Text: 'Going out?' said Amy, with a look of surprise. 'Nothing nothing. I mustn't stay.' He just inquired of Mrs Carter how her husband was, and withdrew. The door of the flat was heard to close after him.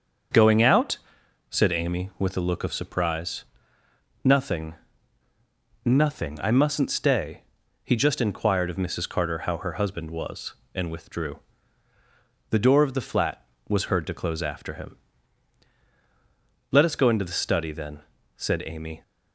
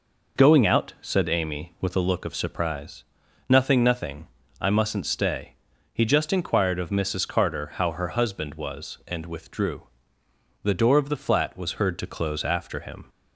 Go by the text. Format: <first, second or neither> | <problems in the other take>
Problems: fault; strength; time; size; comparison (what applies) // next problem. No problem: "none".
second | starts louder than the rest; until 1.8 s; 6.5 dB // pauses between "Nothing" and "nothing"; at 4.7 s; 1.1 s long // goes on to say "Let us go into the study then said Amy"; strong; from 16.7 s on; 2.3 s long